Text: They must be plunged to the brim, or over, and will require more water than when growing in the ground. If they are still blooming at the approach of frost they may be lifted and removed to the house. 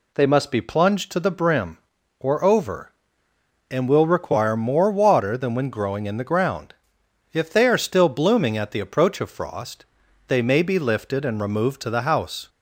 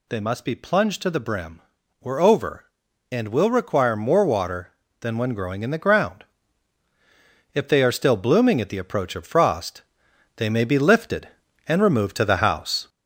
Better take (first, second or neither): first